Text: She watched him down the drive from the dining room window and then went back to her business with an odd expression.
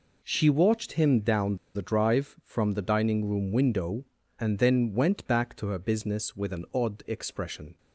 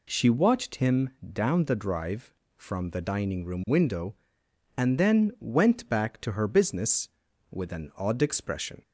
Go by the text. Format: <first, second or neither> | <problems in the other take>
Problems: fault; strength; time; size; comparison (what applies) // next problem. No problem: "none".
second | pauses between "down" and "the"; slight; at 1.5 s; 0.19 s long